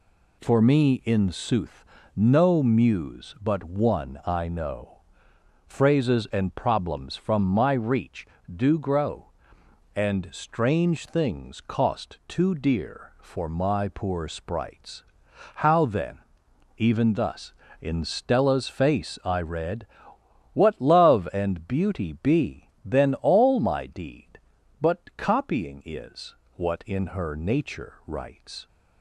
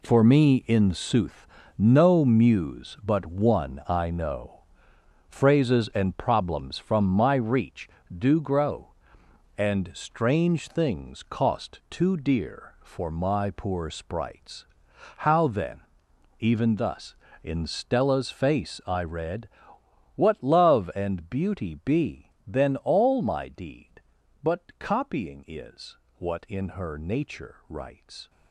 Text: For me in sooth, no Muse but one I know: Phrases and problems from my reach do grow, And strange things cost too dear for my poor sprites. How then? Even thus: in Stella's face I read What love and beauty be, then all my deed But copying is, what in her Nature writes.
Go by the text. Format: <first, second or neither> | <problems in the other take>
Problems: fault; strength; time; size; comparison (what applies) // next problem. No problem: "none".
first | gets quieter; strong; throughout; 10.5 dB // pauses between "read" and "What"; noticeable; at 19.4 s; 0.68 s long; noticeable in the first